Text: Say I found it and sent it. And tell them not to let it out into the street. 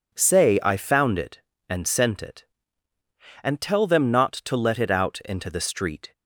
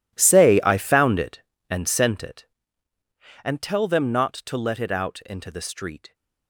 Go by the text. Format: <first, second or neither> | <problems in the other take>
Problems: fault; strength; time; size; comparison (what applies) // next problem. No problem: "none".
first | gets quieter; strong; throughout; 17 dB